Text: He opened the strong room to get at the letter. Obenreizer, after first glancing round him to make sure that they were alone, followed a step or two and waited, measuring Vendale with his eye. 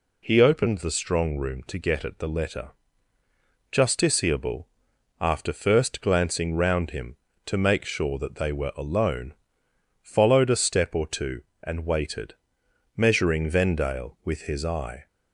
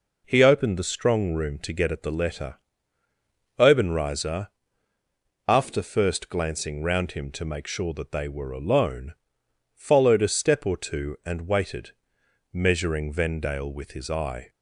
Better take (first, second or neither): second